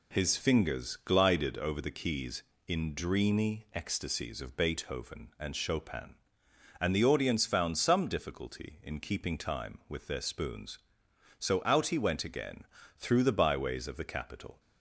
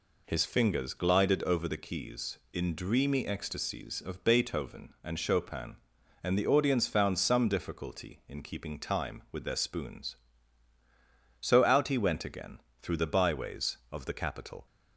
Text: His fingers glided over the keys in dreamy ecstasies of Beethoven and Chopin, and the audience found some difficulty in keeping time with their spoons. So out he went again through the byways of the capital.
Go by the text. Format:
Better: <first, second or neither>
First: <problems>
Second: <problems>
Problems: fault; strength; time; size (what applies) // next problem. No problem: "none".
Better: neither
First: pauses between "again" and "through"; slight; at 12.6 s; 0.32 s long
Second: pauses between "again" and "through"; slight; at 12.5 s; 0.22 s long